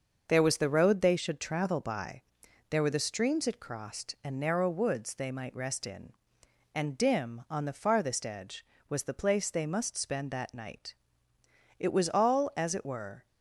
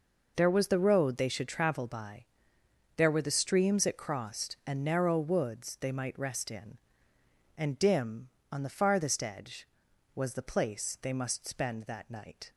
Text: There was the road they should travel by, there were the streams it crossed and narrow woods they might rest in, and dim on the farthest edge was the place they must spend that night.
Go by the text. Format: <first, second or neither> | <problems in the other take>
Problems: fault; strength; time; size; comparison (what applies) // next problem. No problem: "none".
second | starts louder than the rest; until 1.2 s; 6.5 dB // goes on to say "It was all as it were"; from 11.7 s on; 1.4 s long